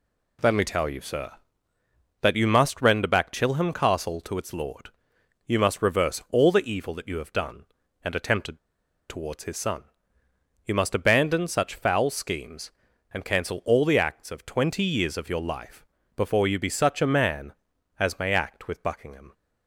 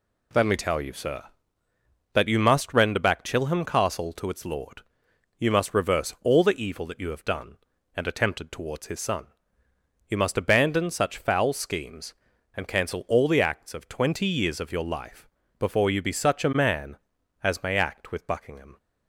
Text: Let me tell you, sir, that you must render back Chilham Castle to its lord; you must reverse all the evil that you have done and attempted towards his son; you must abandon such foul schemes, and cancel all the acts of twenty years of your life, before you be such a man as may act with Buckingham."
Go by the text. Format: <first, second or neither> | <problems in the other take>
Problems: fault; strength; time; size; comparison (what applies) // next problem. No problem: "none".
second | pauses between "attempted" and "towards"; noticeable; at 8.5 s; 0.50 s long